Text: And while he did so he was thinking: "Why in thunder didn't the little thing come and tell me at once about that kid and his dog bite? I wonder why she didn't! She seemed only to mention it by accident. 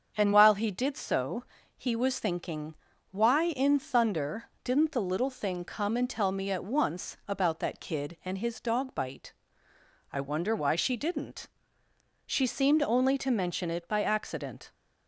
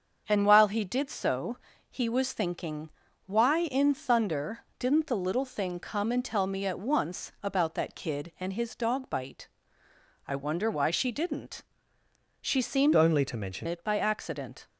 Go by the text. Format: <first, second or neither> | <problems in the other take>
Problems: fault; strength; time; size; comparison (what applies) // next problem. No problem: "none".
first | starts louder than the rest; until 1.2 s; 7 dB; also in the first // pauses between "so" and "he"; slight; at 1.5 s; 0.34 s long; slight in the first // changes voice from "only" to "mention"; from 12.9 to 13.6 s; 0.7 s long